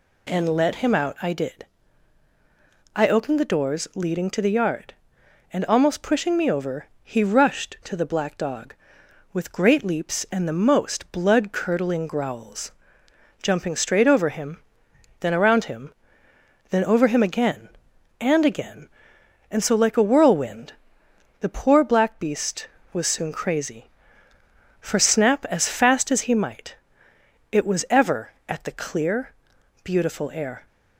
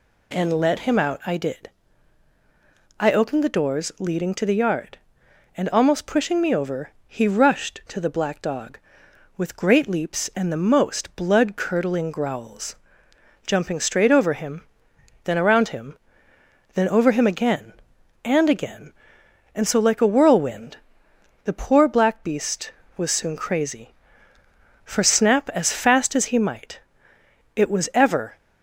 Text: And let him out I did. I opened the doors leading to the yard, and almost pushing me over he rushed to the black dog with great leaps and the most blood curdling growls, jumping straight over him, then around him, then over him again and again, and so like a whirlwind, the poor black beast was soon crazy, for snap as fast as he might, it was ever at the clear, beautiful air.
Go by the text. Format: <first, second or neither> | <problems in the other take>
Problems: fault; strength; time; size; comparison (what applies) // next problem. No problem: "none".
first | pauses between "over" and "he"; slight; at 6.8 s; 0.16 s long; slight in the first // stops before "at the clear beautiful air"; at 28.3 s